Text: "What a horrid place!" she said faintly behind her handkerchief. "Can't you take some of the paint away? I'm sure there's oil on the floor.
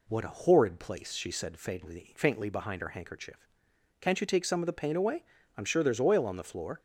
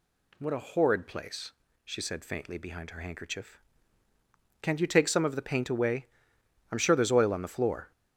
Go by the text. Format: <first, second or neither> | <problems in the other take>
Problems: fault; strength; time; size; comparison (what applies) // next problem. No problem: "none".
second | says "faintly" twice; at 2.1 s